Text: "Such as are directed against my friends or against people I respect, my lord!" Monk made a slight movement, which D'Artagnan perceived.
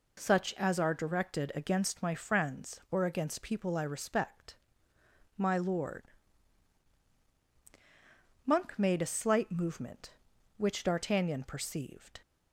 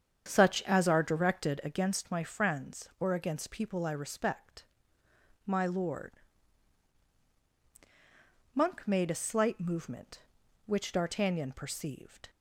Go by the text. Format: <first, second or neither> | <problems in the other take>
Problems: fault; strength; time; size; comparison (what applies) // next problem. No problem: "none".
first | starts louder than the rest; strong; until 1.6 s; 8 dB